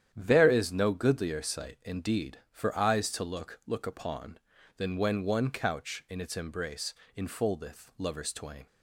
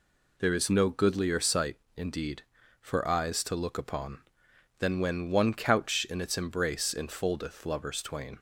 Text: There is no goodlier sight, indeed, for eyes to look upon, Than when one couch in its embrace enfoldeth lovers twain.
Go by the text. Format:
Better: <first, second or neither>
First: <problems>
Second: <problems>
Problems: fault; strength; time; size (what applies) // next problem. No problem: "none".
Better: second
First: starts louder than the rest; strong; until 1.1 s; 10 dB // says "look" twice; at 3.6 s // pauses between "embrace" and "enfoldeth"; slight; at 6.9 s; 0.24 s long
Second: none